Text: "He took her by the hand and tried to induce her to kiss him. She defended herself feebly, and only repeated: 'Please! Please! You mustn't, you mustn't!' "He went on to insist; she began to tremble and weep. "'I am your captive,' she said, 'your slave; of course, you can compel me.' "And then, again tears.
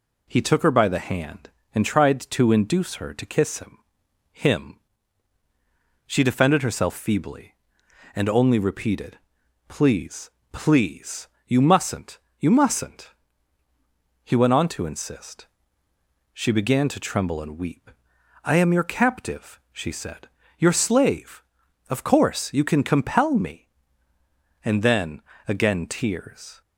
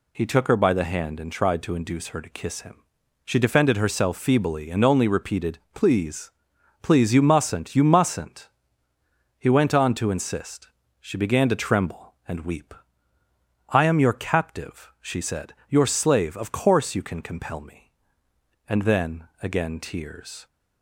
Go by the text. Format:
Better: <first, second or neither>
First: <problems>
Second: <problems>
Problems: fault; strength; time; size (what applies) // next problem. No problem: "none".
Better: second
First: says "him" twice; at 4.3 s // pauses between "compel" and "me"; slight; at 23.3 s; 0.16 s long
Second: none